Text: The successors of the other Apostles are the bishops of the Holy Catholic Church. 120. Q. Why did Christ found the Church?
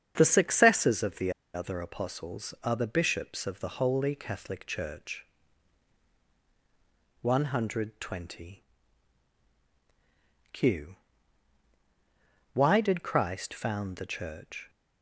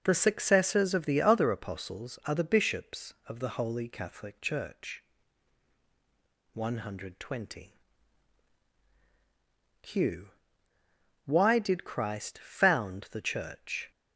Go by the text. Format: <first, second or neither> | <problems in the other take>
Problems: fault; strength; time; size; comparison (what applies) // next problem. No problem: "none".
second | starts louder than the rest; strong; until 1.1 s; 7.5 dB // pauses between "the" and "other"; slight; at 1.3 s; 0.24 s long